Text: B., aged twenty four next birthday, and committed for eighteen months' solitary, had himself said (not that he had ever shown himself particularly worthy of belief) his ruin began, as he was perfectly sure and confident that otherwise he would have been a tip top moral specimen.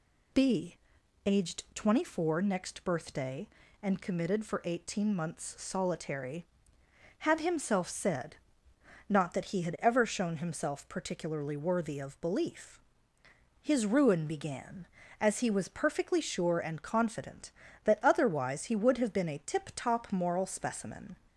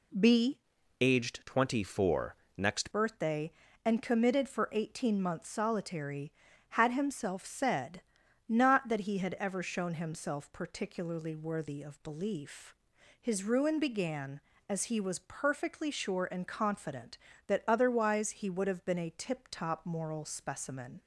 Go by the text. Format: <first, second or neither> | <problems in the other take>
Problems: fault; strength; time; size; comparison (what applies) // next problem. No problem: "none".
first | changes voice from "aged" to "next"; from 0.9 to 2.9 s; 2.0 s long // pauses between "four" and "next"; slight; at 2.3 s; 0.22 s long